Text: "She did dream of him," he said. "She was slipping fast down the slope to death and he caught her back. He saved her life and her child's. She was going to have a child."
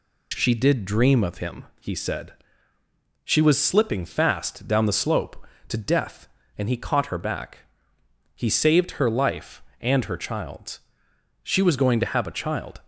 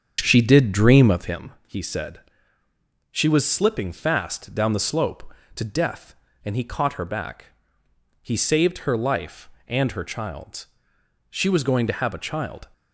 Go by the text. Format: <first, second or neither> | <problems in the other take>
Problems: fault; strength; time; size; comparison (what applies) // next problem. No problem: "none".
first | starts louder than the rest; strong; until 1.5 s; 7.5 dB